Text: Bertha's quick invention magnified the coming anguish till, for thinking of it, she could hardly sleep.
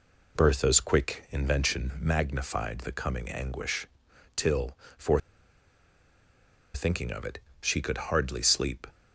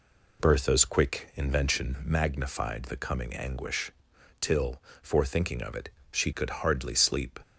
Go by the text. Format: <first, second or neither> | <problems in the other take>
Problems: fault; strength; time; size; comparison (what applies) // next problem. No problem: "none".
second | pauses between "anguish" and "till"; noticeable; at 3.8 s; 0.50 s long; noticeable in the second // pauses between "for" and "thinking"; strong; at 5.1 s; 1.5 s long